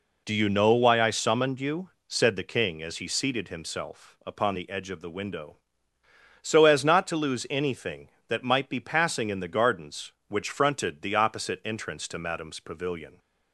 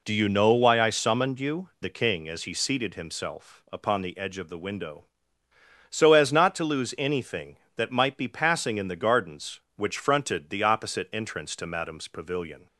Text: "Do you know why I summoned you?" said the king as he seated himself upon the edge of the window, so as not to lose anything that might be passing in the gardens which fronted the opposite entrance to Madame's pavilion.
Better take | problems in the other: first | skips "said"; at 1.7 s

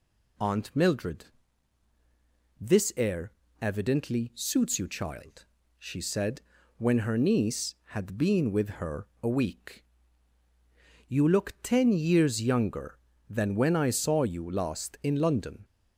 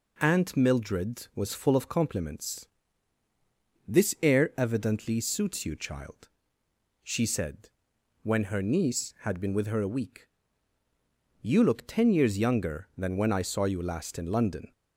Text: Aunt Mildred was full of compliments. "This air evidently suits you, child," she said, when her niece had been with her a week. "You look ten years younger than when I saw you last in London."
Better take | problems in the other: second | skips "was full of compliments"; at 1.9 s // pauses between "air" and "evidently"; slight; at 3.3 s; 0.26 s long // pauses between "her" and "a"; slight; at 9.0 s; 0.16 s long

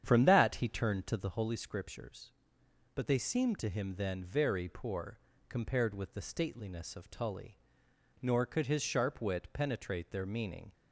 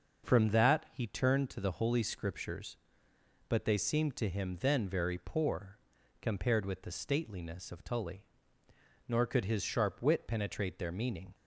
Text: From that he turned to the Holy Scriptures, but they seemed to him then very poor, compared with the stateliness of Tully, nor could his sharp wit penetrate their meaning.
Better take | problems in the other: second | starts louder than the rest; strong; until 1.4 s; 9 dB

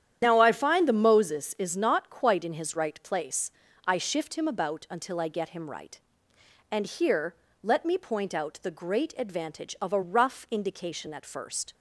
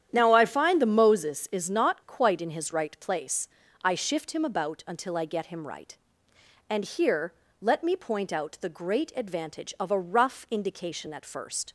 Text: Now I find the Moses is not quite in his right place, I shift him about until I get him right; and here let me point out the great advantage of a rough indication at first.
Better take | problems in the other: second | loses the start of "Now"; at 0.2 s; 45 ms // starts louder than the rest; strong; until 1.2 s; 9.5 dB; strong in the second // pauses between "here" and "let"; slight; at 7.3 s; 0.28 s long; slight in the second

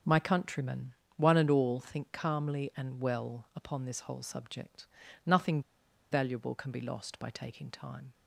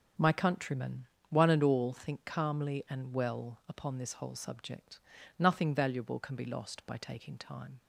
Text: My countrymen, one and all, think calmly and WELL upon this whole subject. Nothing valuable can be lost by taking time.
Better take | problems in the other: second | starts louder than the rest; until 1.3 s; 7 dB; strong in the second // pauses between "Nothing" and "valuable"; noticeable; at 5.6 s; 0.49 s long

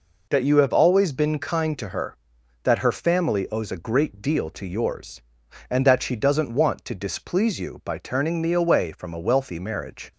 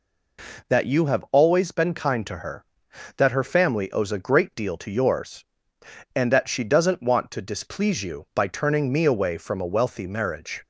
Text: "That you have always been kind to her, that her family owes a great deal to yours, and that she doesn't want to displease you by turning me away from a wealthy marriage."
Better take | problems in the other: neither | none

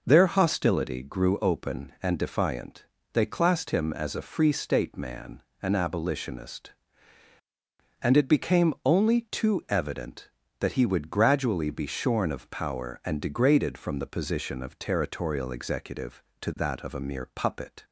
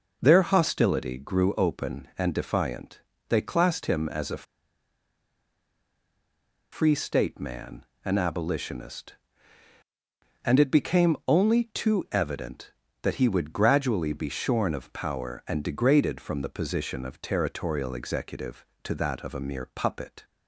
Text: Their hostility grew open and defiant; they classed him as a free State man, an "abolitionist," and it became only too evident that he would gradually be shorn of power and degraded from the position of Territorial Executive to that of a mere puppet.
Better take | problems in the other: first | pauses between "a" and "free"; strong; at 4.4 s; 2.2 s long

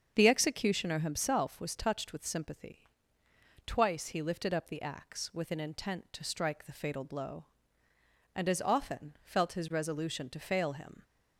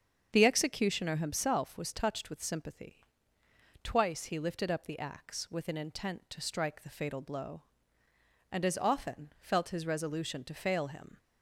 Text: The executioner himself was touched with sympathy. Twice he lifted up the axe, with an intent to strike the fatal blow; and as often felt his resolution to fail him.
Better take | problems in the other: neither | starts louder than the rest; the same in both

